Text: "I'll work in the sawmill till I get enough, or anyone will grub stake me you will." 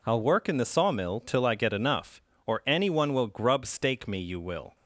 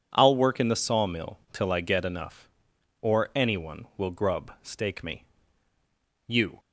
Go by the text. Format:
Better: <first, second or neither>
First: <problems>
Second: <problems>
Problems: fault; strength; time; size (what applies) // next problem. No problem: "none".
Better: first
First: none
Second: pauses between "me" and "you"; at 5.2 s; 1.0 s long // stops before "will"; at 6.5 s